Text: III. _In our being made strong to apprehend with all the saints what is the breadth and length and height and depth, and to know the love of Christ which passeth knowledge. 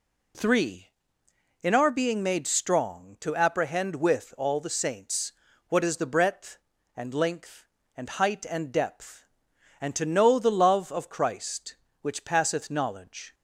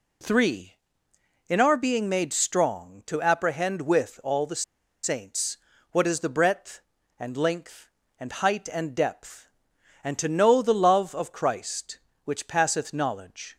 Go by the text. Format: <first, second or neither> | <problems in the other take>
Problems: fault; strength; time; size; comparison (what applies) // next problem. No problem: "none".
first | pauses between "the" and "saints"; at 4.6 s; 0.41 s long // pauses between "saints" and "what"; slight; at 5.5 s; 0.34 s long; slight in the first